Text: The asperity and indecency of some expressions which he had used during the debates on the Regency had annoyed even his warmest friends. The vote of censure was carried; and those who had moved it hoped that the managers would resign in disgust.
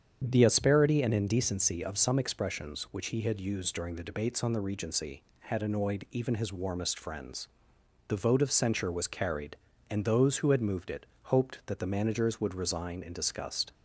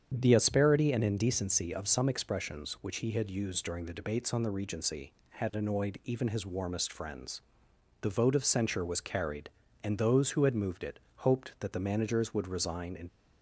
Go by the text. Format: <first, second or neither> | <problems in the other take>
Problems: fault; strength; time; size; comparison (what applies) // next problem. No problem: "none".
first | starts louder than the rest; strong; until 1.1 s; 8 dB; strong in the first // pauses between "it" and "hoped"; slight; at 10.9 s; 0.16 s long; slight in the first // stops before "disgust"; at 13.0 s